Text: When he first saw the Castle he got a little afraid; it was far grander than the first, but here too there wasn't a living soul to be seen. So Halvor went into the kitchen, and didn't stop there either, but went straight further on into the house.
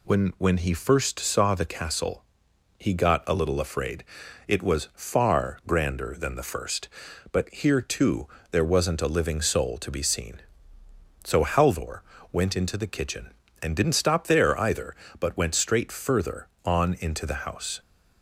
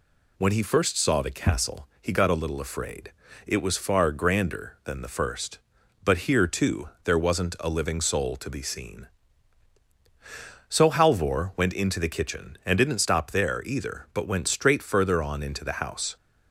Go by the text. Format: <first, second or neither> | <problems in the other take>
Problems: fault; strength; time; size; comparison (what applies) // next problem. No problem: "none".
second | says "When" twice; at 0.3 s // pauses between "Castle" and "he"; noticeable; at 2.2 s; 0.56 s long // pauses between "too" and "there"; slight; at 8.2 s; 0.24 s long; slight in the second // pauses between "Halvor" and "went"; slight; at 12.0 s; 0.30 s long